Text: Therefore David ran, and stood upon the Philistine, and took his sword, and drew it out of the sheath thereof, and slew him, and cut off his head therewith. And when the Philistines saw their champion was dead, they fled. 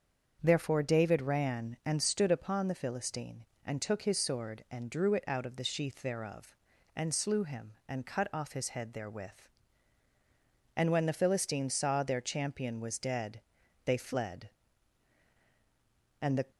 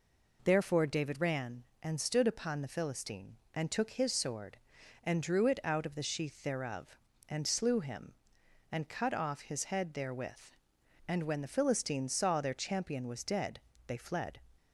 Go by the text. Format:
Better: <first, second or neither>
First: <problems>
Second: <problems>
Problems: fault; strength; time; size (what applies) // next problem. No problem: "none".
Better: second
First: starts louder than the rest; until 1.4 s; 7 dB // goes on to say "And the"; slight; from 16.2 s on; 0.30 s long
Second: none